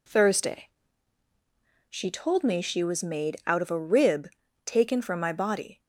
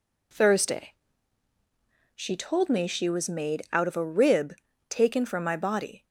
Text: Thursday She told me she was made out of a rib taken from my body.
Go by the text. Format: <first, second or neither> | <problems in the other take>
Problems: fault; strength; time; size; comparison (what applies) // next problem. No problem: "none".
neither | pauses between "Thursday" and "She"; the same in both // pauses between "rib" and "taken"; slight; the same in both